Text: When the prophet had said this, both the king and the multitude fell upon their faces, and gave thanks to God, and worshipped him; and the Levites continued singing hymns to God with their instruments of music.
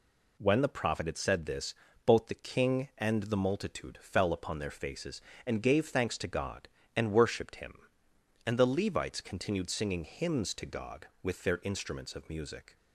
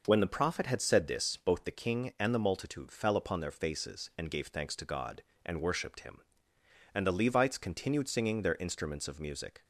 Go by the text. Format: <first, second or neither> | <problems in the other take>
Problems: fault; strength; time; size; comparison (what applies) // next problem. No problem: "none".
first | skips "hymns to God with"; at 8.4 s